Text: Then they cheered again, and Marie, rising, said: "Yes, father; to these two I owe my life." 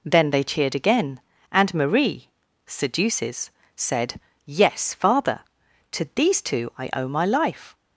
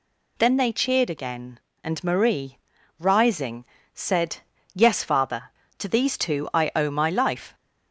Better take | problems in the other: second | says "seduces" for "rising"; at 2.6 s

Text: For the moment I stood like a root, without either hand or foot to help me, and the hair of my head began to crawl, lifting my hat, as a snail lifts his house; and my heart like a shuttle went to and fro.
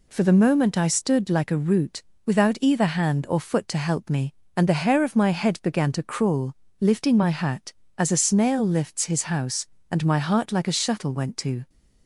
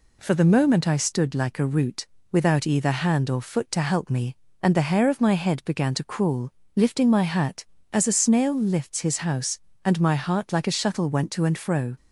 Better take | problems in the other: second | stops before "and fro"; at 11.6 s

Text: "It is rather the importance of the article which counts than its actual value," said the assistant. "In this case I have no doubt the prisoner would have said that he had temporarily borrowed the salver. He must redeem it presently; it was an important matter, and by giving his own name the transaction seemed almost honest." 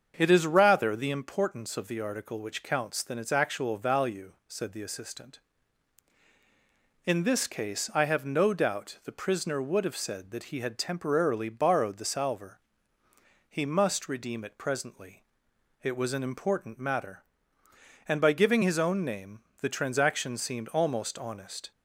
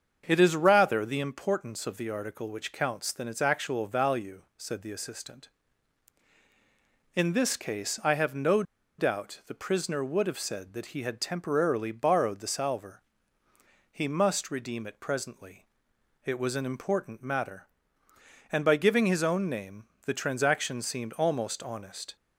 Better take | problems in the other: first | starts louder than the rest; until 1.2 s; 7 dB; also in the first // pauses between "no" and "doubt"; slight; at 8.6 s; 0.36 s long // pauses between "name" and "the"; slight; at 19.8 s; 0.22 s long; slight in the first

